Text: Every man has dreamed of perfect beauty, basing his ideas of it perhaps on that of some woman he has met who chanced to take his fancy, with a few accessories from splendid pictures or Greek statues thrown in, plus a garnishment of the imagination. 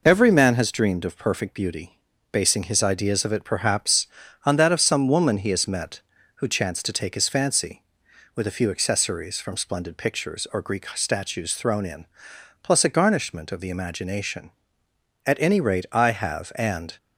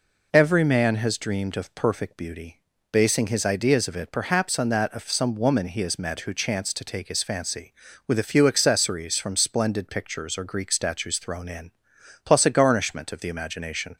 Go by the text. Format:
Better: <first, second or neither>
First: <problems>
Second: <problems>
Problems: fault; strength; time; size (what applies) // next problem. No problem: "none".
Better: second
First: goes on to say "At any rate I have and"; strong; from 15.2 s on; 1.7 s long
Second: none